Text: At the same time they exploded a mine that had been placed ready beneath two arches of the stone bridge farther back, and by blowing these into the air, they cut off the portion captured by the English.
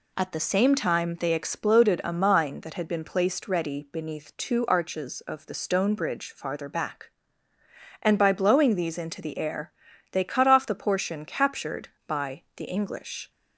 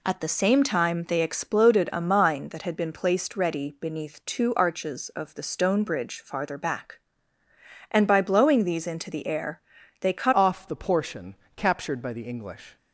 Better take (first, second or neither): first